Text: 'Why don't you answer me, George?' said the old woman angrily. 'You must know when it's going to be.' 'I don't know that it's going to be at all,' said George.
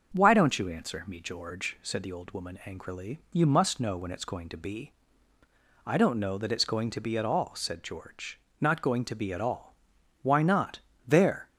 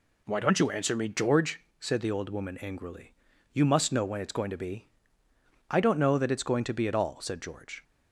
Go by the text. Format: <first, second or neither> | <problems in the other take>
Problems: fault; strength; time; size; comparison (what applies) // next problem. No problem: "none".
second | starts louder than the rest; until 1.1 s; 6 dB // goes on to say "Not going to be at all Why not There"; strong; from 8.6 s on; 2.8 s long